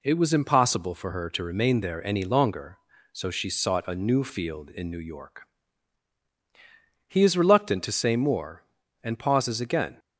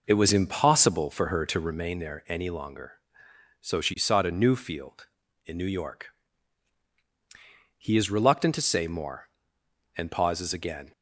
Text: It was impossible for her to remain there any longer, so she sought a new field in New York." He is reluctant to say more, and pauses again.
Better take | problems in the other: first | starts louder than the rest; noticeable; until 2.0 s; 5 dB

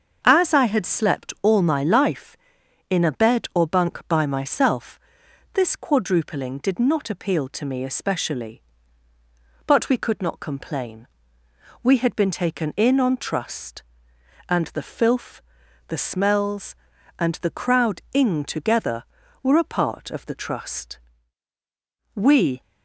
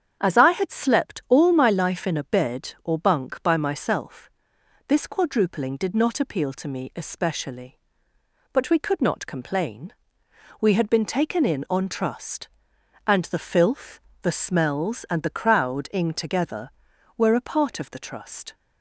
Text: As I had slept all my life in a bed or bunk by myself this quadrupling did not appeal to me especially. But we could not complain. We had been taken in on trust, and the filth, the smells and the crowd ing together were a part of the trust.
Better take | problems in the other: second | starts louder than the rest; until 1.2 s; 6.5 dB; strong in the second // pauses between "myself" and "this"; noticeable; at 4.9 s; 0.54 s long; noticeable in the second // goes on to say "We"; slight; from 22.1 s on; 0.46 s long

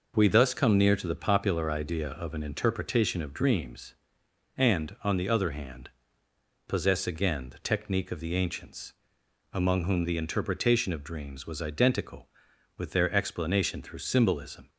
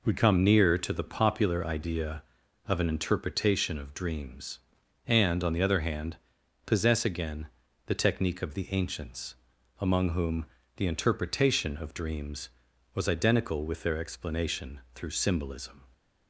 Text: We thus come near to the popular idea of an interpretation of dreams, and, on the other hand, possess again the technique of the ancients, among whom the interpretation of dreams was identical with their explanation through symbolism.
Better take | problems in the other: first | skips "thus"; at 0.1 s // pauses between "again" and "the"; at 7.4 s; 0.38 s long // pauses between "whom" and "the"; slight; at 10.4 s; 0.32 s long

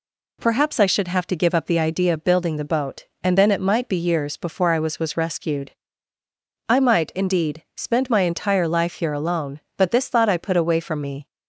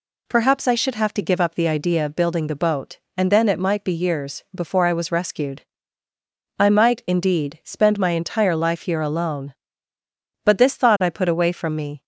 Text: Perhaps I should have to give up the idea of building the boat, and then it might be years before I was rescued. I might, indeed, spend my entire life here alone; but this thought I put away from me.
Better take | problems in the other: second | says "was" twice; at 4.9 s

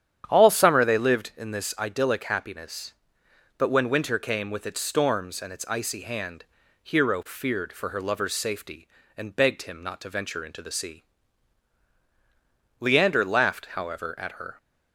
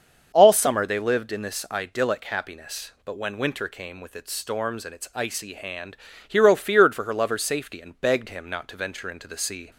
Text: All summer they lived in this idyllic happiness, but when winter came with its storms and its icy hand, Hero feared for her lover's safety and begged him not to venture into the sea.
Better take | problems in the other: second | starts louder than the rest; strong; until 1.2 s; 9.5 dB; also in the second // goes on to say "Leander laughed however at her"; strong; from 12.7 s on; 1.7 s long

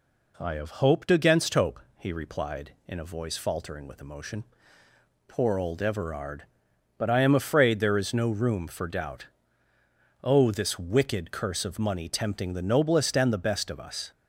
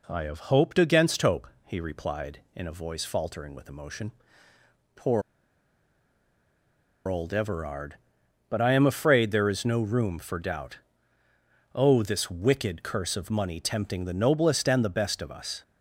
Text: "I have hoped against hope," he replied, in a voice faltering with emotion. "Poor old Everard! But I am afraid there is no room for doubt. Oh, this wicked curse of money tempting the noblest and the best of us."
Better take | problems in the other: first | pauses between "Poor" and "old"; strong; at 5.2 s; 1.8 s long

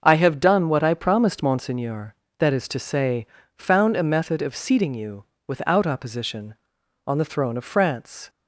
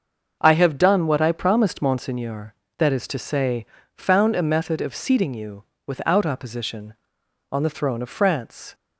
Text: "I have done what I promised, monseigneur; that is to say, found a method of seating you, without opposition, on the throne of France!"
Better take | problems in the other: neither | starts louder than the rest; the same in both

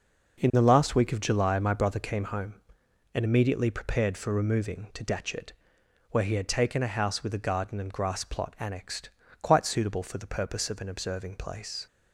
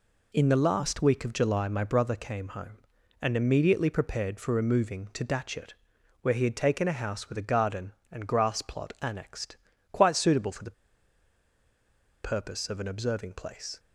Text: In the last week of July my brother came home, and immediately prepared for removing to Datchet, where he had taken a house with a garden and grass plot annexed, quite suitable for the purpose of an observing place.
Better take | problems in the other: first | pauses between "the" and "purpose"; strong; at 10.7 s; 1.5 s long

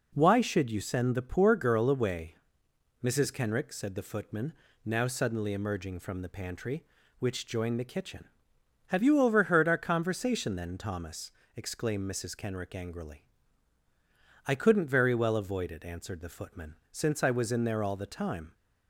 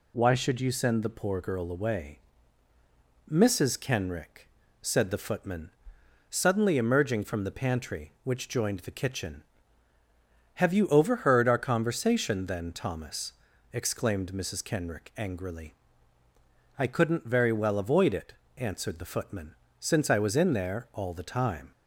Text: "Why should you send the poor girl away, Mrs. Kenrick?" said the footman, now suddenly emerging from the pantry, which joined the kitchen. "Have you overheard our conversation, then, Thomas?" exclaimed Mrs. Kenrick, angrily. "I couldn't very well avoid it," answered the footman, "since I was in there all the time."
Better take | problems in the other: first | skips "now"; at 6.0 s

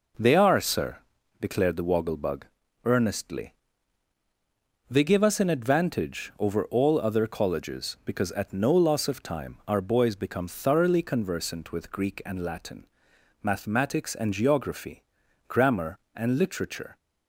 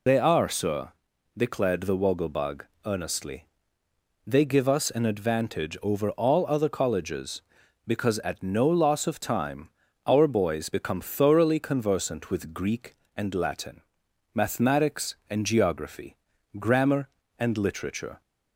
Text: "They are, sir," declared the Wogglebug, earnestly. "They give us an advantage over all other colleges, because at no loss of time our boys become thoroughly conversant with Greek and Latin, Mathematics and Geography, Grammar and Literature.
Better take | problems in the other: first | loses the start of "They"; at 0.0 s; 80 ms // pauses between "time" and "our"; at 9.6 s; 0.38 s long

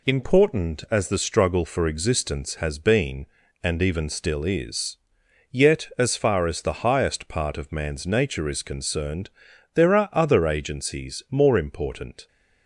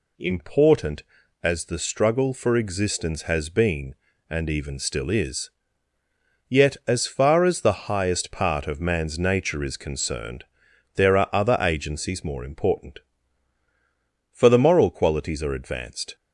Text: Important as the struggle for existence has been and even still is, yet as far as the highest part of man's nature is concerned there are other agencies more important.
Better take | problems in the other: first | pauses between "concerned" and "there"; noticeable; at 10.4 s; 0.52 s long; noticeable in the first // goes on to say "For the moral qualities are advanced"; strong; from 14.3 s on; 1.8 s long

